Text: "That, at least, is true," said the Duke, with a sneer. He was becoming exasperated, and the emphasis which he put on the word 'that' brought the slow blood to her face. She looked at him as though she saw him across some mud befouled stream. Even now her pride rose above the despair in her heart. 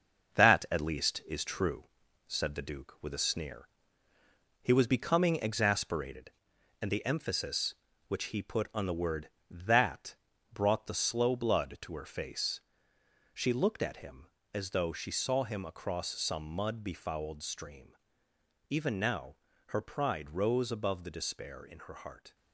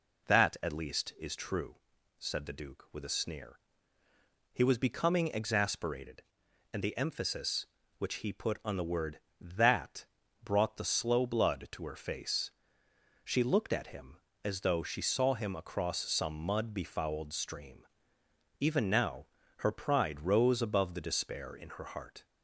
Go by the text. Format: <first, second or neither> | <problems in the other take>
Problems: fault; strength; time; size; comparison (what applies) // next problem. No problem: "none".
second | gets quieter; noticeable; throughout; 6 dB // pauses between "that" and "brought"; at 10.1 s; 0.38 s long; also in the second // pauses between "now" and "her"; slight; at 19.3 s; 0.32 s long; slight in the second